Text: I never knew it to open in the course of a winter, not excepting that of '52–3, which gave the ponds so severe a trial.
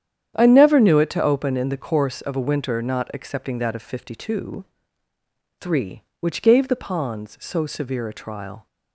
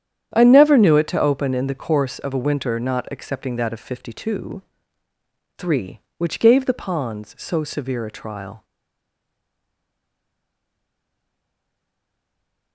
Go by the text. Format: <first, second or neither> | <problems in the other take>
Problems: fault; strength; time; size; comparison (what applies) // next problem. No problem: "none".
first | starts louder than the rest; strong; until 1.3 s; 9.5 dB; strong in the first // stays silent after the last word; strong; from 8.6 s on; 4.1 s long